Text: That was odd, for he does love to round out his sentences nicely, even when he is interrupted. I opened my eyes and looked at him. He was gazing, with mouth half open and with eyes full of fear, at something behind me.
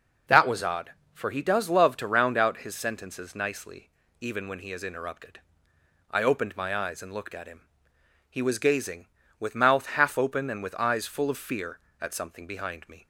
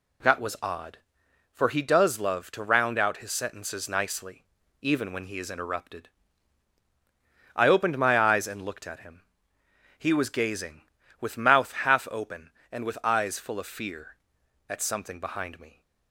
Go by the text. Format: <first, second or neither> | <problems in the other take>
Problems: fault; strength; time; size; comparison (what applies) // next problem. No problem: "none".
neither | none